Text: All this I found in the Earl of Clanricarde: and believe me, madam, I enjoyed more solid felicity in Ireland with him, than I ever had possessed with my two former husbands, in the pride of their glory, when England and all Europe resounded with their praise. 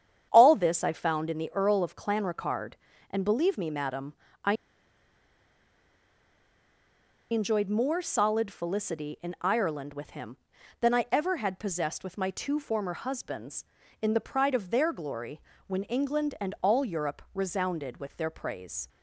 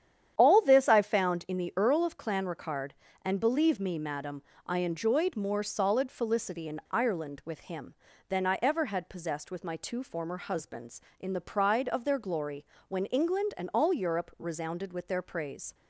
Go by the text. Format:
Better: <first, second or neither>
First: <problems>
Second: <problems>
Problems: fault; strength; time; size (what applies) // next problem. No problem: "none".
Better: second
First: starts louder than the rest; strong; until 1.3 s; 8.5 dB // pauses between "I" and "enjoyed"; strong; at 4.5 s; 2.7 s long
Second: starts louder than the rest; strong; until 1.3 s; 9.5 dB